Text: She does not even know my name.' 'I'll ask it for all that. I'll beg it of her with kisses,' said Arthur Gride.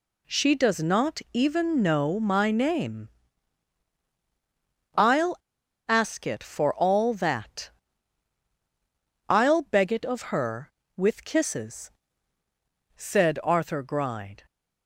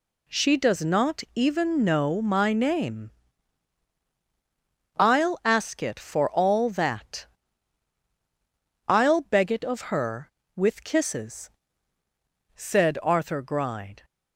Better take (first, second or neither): second